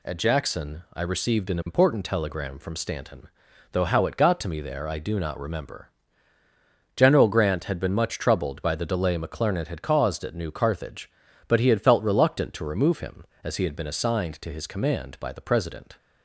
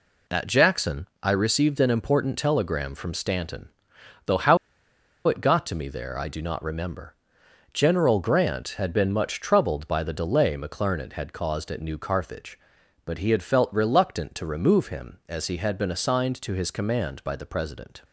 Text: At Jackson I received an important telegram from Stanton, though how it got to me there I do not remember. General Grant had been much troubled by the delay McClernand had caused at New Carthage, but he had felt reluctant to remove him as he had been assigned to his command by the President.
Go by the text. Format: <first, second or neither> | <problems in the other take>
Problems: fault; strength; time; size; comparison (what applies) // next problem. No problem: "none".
first | pauses between "Jackson" and "I"; slight; at 1.0 s; 0.16 s long // pauses between "how" and "it"; noticeable; at 4.5 s; 0.69 s long